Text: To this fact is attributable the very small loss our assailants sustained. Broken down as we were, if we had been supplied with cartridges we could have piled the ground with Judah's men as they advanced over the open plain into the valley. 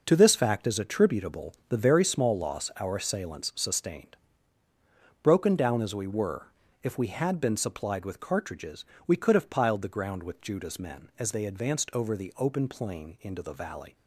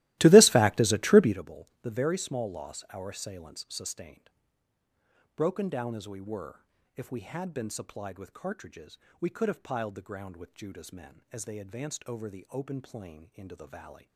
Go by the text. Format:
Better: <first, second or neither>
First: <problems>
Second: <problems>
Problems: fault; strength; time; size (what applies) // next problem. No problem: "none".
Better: first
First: pauses between "cartridges" and "we"; slight; at 8.8 s; 0.22 s long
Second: starts louder than the rest; strong; until 1.4 s; 17 dB // pauses between "cartridges" and "we"; slight; at 8.9 s; 0.22 s long